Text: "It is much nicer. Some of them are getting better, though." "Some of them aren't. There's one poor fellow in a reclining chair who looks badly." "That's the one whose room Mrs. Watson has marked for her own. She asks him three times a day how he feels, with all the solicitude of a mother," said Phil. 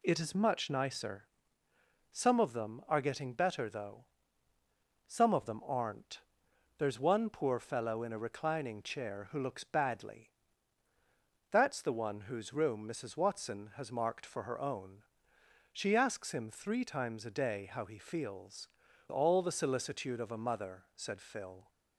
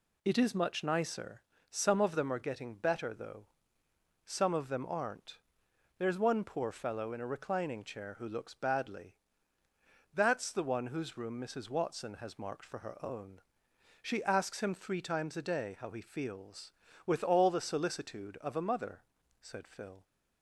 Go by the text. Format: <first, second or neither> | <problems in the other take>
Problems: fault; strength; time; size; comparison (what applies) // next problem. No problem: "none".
second | skips "with"; at 18.8 s